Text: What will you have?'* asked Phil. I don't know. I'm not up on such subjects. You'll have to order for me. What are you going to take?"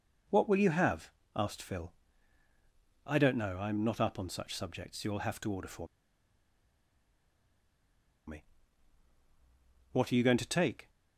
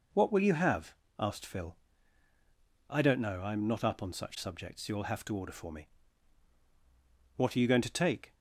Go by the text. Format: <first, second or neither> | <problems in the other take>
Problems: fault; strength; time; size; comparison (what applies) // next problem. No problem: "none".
second | pauses between "for" and "me"; strong; at 5.8 s; 2.4 s long